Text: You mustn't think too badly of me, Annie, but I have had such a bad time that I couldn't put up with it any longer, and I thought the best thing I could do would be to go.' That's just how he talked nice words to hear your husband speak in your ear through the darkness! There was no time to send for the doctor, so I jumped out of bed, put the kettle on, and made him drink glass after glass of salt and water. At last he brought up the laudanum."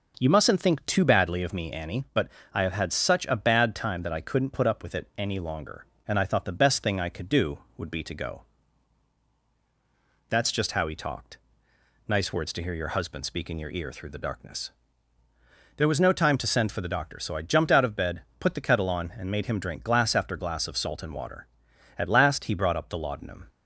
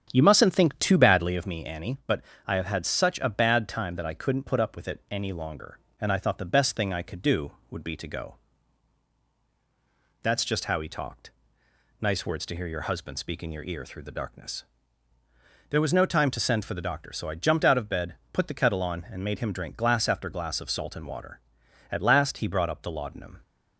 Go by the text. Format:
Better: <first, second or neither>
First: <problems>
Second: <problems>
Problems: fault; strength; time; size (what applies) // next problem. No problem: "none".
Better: first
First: pauses between "but" and "I"; slight; at 2.2 s; 0.26 s long // pauses between "talked" and "nice"; noticeable; at 11.3 s; 0.70 s long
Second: starts louder than the rest; strong; until 1.5 s; 8 dB // pauses between "but" and "I"; slight; at 2.2 s; 0.26 s long // pauses between "talked" and "nice"; noticeable; at 11.3 s; 0.70 s long